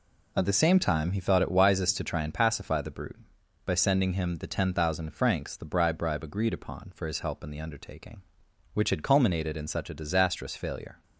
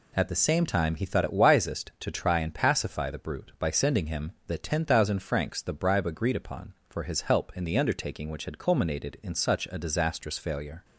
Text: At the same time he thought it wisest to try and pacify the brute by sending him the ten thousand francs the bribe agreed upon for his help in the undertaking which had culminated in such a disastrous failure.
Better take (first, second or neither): second